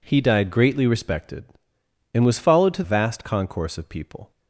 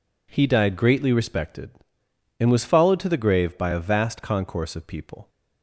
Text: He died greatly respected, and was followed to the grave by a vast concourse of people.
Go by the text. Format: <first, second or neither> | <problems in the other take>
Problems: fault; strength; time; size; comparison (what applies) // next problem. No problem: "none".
second | skips "the grave by a"; at 2.8 s